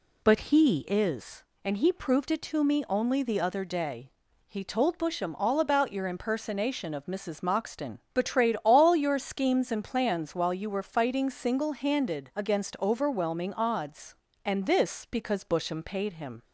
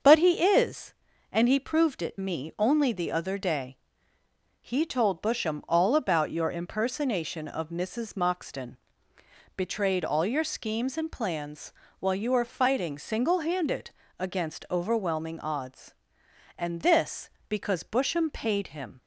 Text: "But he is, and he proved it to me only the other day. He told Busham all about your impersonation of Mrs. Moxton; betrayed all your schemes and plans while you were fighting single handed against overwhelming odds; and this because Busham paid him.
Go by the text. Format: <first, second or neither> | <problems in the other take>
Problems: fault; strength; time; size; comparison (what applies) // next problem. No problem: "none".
first | starts louder than the rest; until 1.3 s; 6.5 dB // skips "to"; at 2.1 s // pauses between "plans" and "while"; slight; at 11.7 s; 0.28 s long // pauses between "handed" and "against"; slight; at 13.9 s; 0.26 s long